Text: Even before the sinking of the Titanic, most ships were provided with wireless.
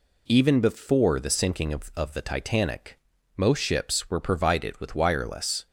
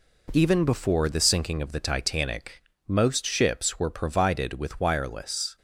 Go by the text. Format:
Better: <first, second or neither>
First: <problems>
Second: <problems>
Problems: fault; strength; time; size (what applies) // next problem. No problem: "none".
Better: second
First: says "of" twice; at 1.9 s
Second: none